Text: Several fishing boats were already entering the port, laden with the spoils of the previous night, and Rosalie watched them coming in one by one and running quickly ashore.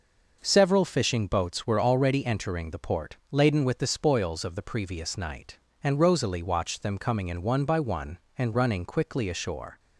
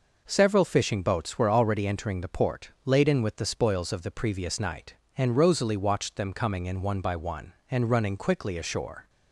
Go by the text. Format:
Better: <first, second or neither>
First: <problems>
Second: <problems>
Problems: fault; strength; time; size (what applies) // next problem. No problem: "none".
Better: neither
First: none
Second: none